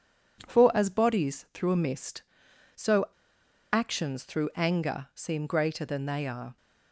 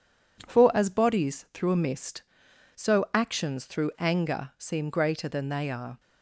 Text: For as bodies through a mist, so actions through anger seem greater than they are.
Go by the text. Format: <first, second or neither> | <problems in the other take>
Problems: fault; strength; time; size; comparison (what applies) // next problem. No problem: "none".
second | pauses between "so" and "actions"; noticeable; at 3.0 s; 0.66 s long